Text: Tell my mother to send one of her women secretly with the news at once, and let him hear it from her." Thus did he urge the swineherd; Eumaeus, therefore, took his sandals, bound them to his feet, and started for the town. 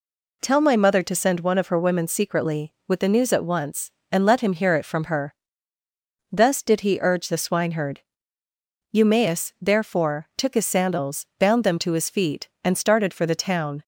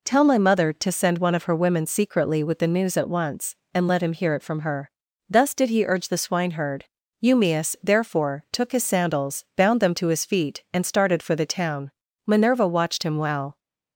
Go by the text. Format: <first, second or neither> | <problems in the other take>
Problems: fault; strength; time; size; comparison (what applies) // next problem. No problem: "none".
first | goes on to say "Minerva watched him well"; from 12.2 s on; 1.3 s long